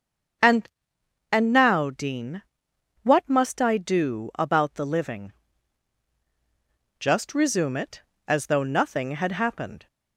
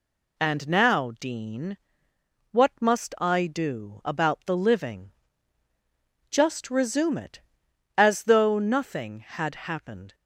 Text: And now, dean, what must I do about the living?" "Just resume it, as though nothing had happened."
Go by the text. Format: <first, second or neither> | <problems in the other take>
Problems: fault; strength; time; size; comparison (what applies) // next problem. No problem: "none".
second | starts louder than the rest; strong; until 2.0 s; 7 dB // says "And" twice; at 1.3 s